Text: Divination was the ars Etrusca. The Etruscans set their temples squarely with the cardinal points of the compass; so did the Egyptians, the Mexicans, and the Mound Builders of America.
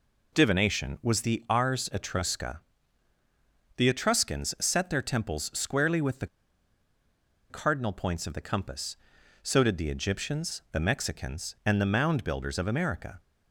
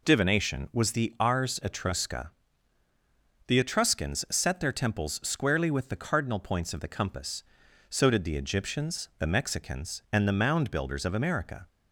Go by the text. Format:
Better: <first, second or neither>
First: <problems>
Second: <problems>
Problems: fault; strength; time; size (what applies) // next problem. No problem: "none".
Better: second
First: pauses between "the" and "cardinal"; at 6.2 s; 1.2 s long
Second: none